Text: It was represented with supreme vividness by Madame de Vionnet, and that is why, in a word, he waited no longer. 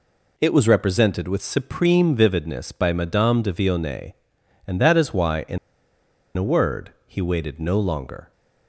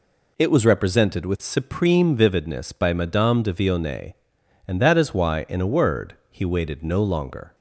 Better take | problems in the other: second | pauses between "in" and "a"; noticeable; at 5.5 s; 0.79 s long

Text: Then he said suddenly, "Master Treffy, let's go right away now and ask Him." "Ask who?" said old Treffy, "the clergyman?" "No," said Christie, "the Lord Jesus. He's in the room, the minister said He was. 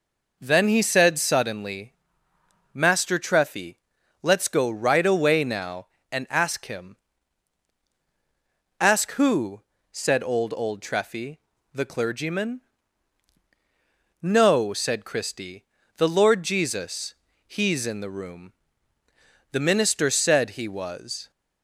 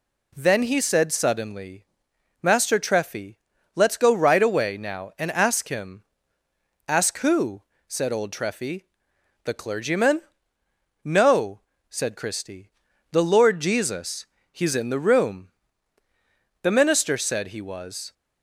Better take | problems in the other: second | says "old" twice; at 10.5 s

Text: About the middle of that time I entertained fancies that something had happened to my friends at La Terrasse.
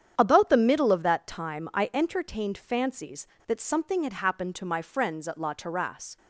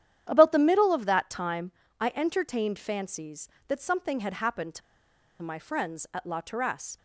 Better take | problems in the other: first | starts louder than the rest; strong; until 1.3 s; 10 dB; strong in the first // pauses between "time" and "I"; slight; at 1.7 s; 0.30 s long // pauses between "to" and "my"; noticeable; at 4.8 s; 0.62 s long

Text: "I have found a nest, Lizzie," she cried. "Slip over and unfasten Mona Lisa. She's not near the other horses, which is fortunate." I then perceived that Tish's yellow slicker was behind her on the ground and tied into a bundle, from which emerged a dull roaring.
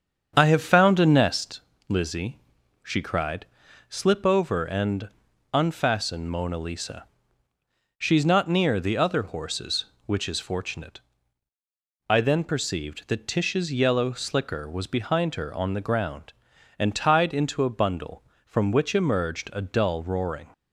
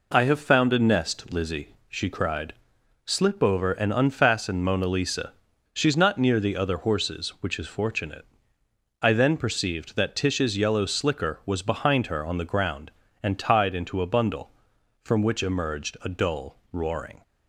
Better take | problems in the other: second | starts louder than the rest; strong; until 1.4 s; 7.5 dB // pauses between "and" and "unfasten"; at 5.0 s; 0.44 s long

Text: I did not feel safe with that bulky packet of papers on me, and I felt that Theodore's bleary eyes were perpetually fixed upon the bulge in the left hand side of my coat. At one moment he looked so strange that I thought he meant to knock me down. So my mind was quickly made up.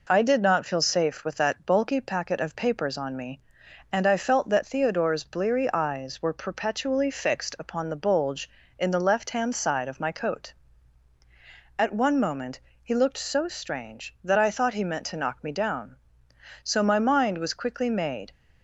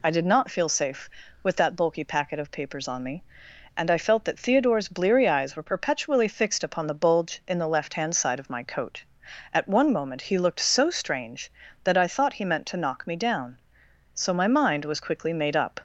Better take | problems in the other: second | pauses between "moment" and "he"; slight; at 12.6 s; 0.24 s long // stops before "up"; at 18.3 s

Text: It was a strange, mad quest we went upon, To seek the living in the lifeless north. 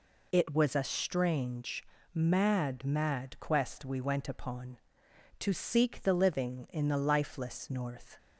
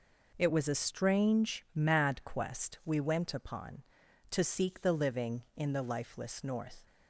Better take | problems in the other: second | says "mad" twice; at 2.8 s

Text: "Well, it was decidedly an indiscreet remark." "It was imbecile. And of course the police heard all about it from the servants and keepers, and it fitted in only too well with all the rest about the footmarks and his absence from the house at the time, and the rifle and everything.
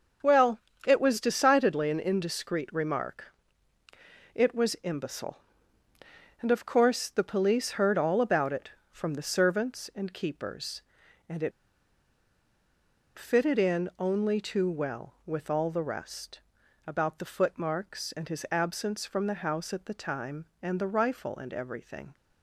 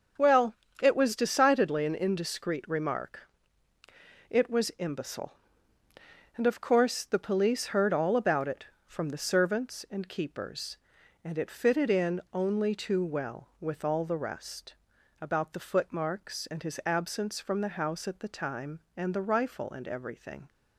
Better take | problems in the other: second | starts louder than the rest; until 1.4 s; 6.5 dB; also in the second // pauses between "it" and "fitted"; strong; at 11.5 s; 1.6 s long // pauses between "rest" and "about"; noticeable; at 16.3 s; 0.46 s long; noticeable in the second

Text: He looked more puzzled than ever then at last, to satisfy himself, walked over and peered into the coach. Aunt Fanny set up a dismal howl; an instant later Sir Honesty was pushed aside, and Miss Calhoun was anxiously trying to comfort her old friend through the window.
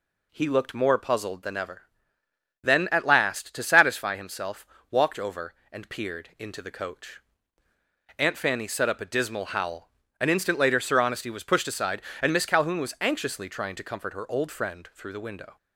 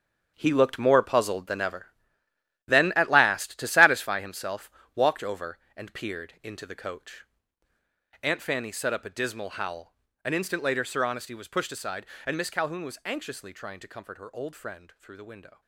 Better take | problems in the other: first | gets quieter; strong; throughout; 12 dB // pauses between "ever" and "then"; noticeable; at 1.8 s; 0.80 s long; noticeable in the first

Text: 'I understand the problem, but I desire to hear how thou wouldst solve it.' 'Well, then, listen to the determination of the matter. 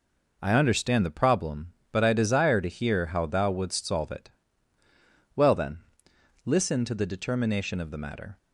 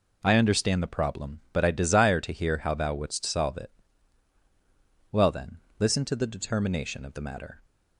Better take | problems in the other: neither | none

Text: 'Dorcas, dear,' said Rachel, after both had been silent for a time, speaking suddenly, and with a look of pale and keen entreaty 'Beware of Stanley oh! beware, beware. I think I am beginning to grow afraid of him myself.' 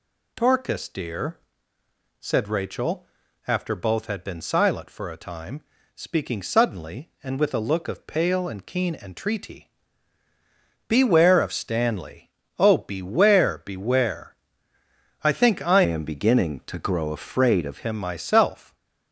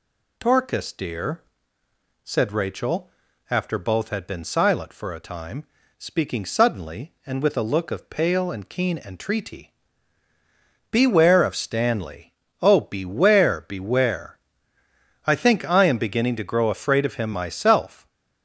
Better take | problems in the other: second | pauses between "entreaty" and "Beware"; at 9.7 s; 1.1 s long; also in the second // pauses between "Stanley" and "oh"; slight; at 12.3 s; 0.28 s long; slight in the second // changes voice from "am" to "of"; from 15.8 to 17.8 s; 2.0 s long

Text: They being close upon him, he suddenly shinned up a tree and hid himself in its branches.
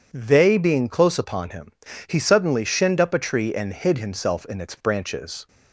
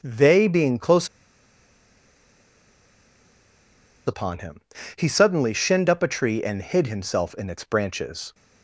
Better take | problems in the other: first | pauses between "close" and "upon"; strong; at 1.0 s; 2.9 s long

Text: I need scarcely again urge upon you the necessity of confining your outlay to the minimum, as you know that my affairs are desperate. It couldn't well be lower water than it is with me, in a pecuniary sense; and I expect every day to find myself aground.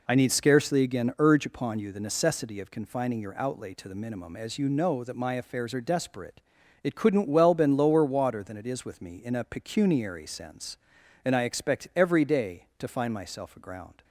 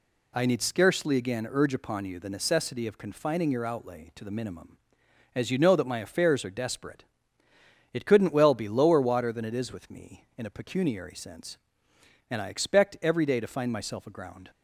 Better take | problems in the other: second | says "been" for "be"; at 7.5 s

